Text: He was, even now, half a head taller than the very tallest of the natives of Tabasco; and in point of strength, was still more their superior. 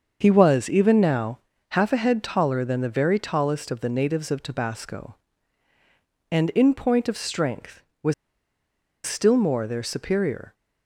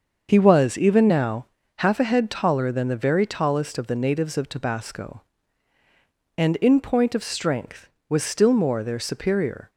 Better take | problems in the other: second | starts louder than the rest; until 1.2 s; 6.5 dB; also in the second // pauses between "was" and "still"; noticeable; at 8.1 s; 0.93 s long

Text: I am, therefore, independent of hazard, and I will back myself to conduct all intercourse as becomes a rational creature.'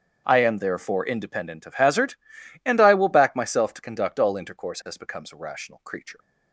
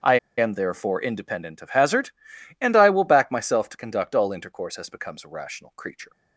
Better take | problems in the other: first | starts louder than the rest; strong; until 1.2 s; 7.5 dB; strong in the first // pauses between "I" and "am"; slight; at 0.1 s; 0.21 s long

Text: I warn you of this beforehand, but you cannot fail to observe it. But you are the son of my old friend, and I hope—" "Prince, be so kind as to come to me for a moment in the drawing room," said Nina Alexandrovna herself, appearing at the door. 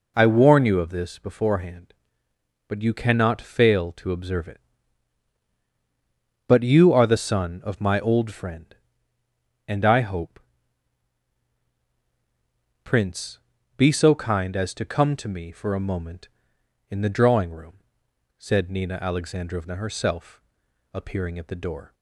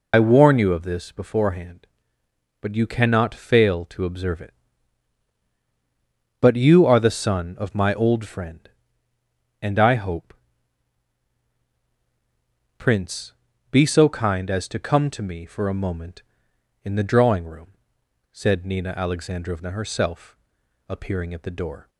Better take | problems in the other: first | loses the start of "I"; at 0.1 s; 45 ms

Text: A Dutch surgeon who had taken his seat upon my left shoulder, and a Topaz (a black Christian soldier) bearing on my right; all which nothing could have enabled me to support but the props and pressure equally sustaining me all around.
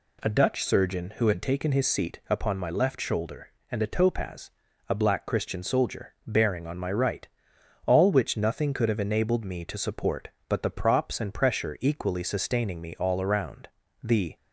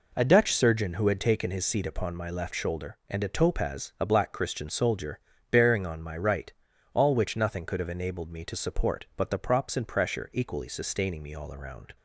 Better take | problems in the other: second | goes on to say "The"; slight; from 14.0 s on; 0.32 s long

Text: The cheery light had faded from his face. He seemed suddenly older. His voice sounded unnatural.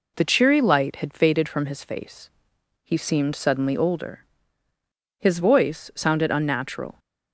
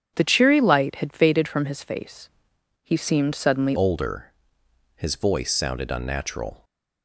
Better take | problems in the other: first | starts louder than the rest; strong; until 1.1 s; 8 dB // changes voice at "older"; from 3.7 s on; 2.9 s long

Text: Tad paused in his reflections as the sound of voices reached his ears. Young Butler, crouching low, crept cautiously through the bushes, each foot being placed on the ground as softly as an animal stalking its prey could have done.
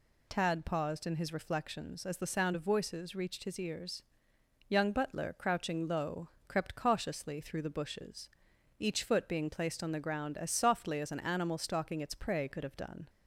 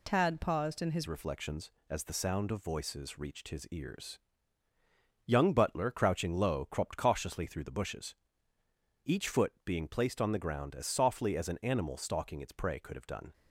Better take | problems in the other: first | changes voice at "reflections"; from 1.0 s on; 12.3 s long

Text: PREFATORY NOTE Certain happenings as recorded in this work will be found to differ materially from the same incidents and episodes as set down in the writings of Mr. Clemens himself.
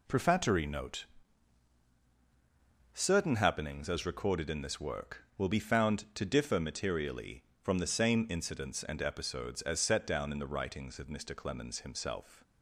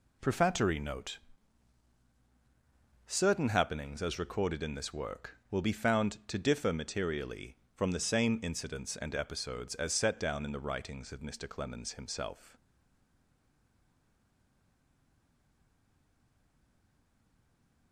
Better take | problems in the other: first | pauses between "NOTE" and "Certain"; strong; at 1.1 s; 1.8 s long; strong in the first // stays silent after the last word; strong; from 12.5 s on; 5.4 s long

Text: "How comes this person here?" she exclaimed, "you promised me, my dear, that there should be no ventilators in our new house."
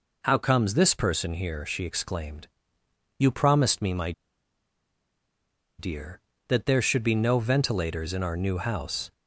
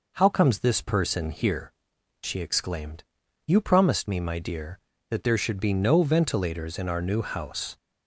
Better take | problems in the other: second | pauses between "my" and "dear"; strong; at 4.1 s; 1.6 s long

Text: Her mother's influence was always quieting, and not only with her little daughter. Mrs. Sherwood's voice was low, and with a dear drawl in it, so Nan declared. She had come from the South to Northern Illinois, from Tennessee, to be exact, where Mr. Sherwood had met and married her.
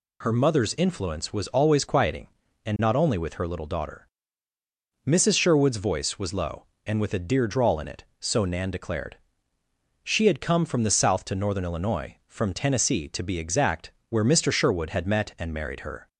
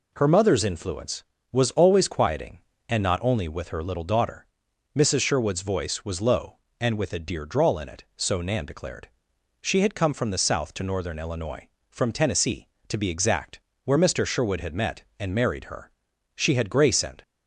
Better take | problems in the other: first | goes on to say "She had grace and"; noticeable; from 16.3 s on; 0.86 s long

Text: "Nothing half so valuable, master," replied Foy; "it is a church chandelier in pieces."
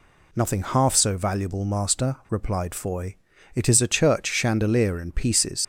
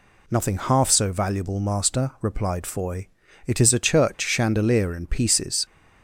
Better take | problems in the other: second | leaves "pieces" unfinished; at 5.6 s; 55 ms

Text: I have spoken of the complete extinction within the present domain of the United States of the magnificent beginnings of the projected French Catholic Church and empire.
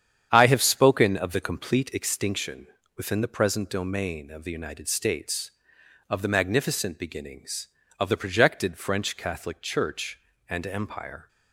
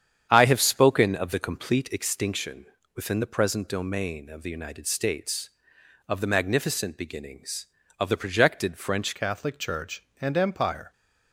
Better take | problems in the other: first | starts louder than the rest; strong; until 1.3 s; 8.5 dB; strong in the first // pauses between "extinction" and "within"; slight; at 2.6 s; 0.32 s long; slight in the first // changes voice at "Catholic"; from 9.1 s on; 1.8 s long

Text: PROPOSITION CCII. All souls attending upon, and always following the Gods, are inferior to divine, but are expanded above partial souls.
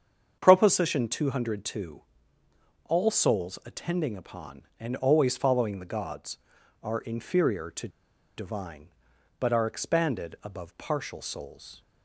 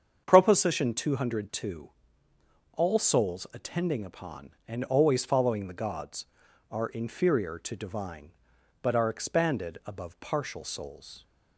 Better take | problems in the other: second | starts louder than the rest; strong; until 1.4 s; 7 dB; strong in the second // pauses between "to" and "divine"; noticeable; at 7.8 s; 0.48 s long

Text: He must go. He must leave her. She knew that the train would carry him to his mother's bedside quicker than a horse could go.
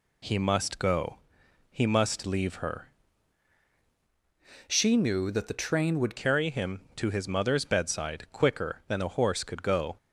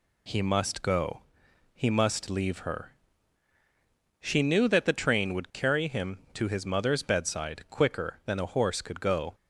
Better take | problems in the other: second | changes voice from "She" to "would"; from 4.6 to 6.1 s; 1.5 s long

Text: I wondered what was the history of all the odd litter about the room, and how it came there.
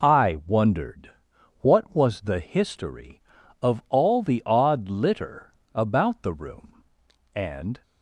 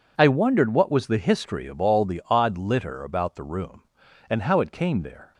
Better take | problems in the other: second | pauses between "wondered" and "what"; noticeable; at 1.1 s; 0.48 s long // pauses between "litter" and "about"; slight; at 5.5 s; 0.26 s long // stops before "how it came there"; at 7.8 s

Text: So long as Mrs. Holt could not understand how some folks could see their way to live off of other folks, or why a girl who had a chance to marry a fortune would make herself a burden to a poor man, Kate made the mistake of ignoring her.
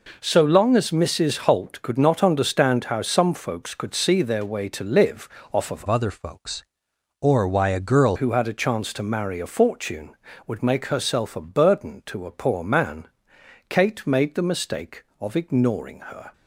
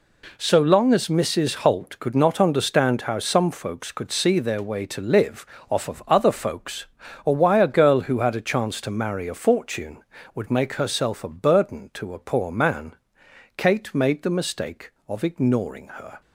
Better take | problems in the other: second | pauses between "live" and "off"; slight; at 5.2 s; 0.26 s long; slight in the second // changes voice from "other" to "girl"; from 5.8 to 8.1 s; 2.3 s long

